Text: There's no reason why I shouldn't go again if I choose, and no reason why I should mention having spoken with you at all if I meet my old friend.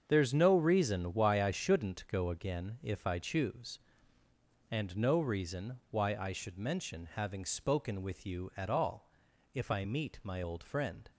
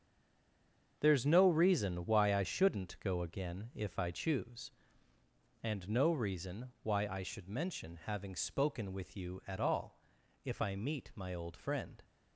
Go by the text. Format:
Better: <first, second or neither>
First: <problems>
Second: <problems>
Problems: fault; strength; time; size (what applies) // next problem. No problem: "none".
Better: first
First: starts louder than the rest; until 1.0 s; 7 dB // pauses between "all" and "if"; noticeable; at 9.0 s; 0.46 s long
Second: stays silent before the first word; until 0.9 s; 0.9 s long // starts louder than the rest; until 2.0 s; 7 dB // pauses between "all" and "if"; noticeable; at 9.9 s; 0.46 s long